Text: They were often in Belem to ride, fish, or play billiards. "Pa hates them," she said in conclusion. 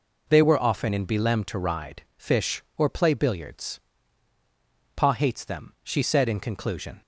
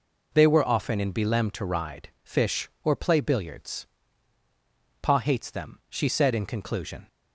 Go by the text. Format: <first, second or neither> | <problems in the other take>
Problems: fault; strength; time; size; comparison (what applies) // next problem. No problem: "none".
neither | none